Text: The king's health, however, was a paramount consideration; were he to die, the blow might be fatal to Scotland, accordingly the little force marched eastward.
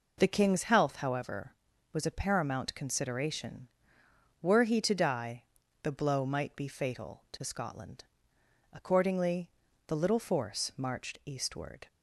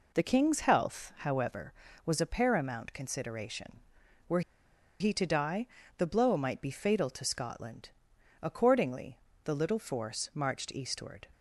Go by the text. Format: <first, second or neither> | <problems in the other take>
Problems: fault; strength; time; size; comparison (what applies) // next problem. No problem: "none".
first | pauses between "were" and "he"; noticeable; at 4.4 s; 0.59 s long // pauses between "accordingly" and "the"; slight; at 9.1 s; 0.28 s long; also in the first